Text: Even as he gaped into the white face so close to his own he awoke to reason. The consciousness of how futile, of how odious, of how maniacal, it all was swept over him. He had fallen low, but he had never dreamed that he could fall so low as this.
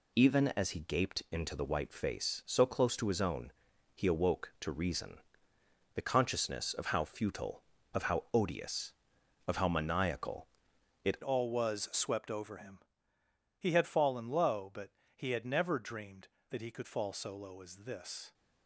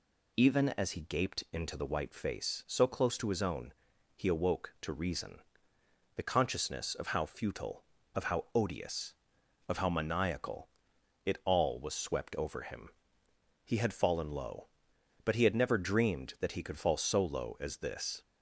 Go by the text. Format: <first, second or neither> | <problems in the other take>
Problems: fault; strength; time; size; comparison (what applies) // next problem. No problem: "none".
second | pauses between "own" and "he"; at 3.5 s; 0.42 s long; also in the second // changes voice at "all"; from 11.2 s on; 7.1 s long // pauses between "but" and "he"; slight; at 14.9 s; 0.24 s long